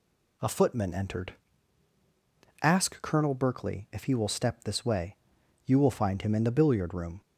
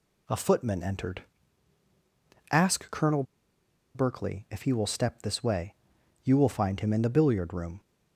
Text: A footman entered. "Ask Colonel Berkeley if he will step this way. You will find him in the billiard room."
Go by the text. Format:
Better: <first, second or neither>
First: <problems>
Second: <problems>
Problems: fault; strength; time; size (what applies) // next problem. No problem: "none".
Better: first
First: none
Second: pauses between "Colonel" and "Berkeley"; noticeable; at 3.2 s; 0.71 s long